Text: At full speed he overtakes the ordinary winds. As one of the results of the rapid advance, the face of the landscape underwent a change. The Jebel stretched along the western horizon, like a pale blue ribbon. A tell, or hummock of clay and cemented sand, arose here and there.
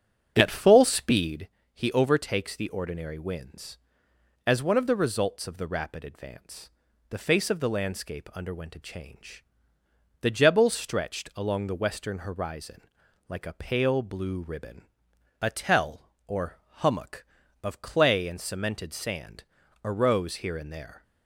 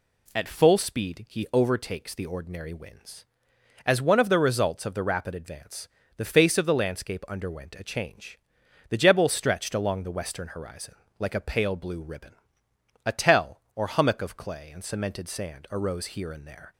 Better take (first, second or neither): second